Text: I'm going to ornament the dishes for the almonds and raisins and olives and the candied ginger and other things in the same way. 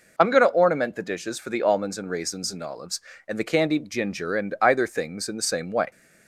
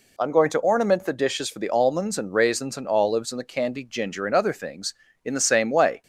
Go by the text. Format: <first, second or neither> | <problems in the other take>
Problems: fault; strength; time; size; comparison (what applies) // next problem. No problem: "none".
second | says "either" for "other"; at 4.6 s